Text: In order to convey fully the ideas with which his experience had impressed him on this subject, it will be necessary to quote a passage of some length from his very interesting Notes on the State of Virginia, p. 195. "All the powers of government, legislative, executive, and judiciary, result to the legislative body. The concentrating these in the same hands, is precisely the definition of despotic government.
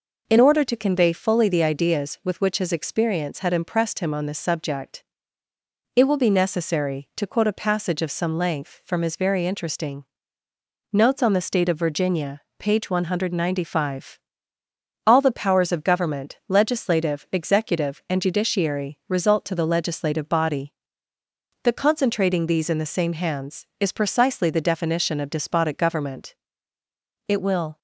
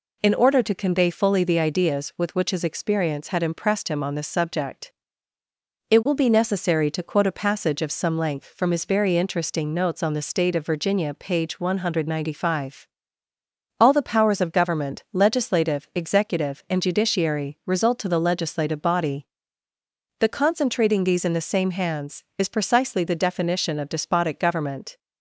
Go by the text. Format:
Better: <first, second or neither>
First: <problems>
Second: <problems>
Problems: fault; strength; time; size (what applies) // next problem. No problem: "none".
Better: second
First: pauses between "interesting" and "Notes"; noticeable; at 10.0 s; 0.90 s long // goes on to say "It will"; from 27.2 s on; 0.52 s long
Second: none